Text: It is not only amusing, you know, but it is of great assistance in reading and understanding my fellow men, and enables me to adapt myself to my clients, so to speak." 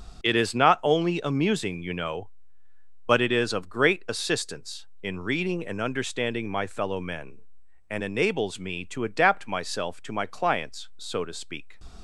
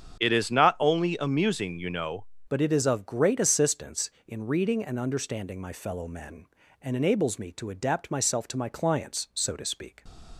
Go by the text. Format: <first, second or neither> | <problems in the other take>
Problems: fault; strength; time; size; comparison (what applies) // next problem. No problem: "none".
first | starts louder than the rest; strong; until 1.2 s; 7.5 dB; also in the first // changes voice at "but"; from 2.4 s on; 7.6 s long